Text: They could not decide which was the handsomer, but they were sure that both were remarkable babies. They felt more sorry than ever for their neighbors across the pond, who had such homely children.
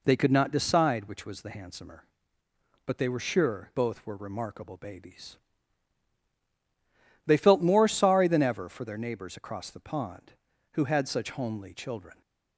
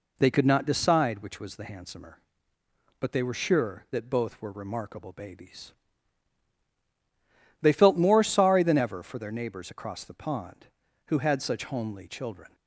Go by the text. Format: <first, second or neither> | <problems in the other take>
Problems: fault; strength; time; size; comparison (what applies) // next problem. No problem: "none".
second | skips "that"; at 3.7 s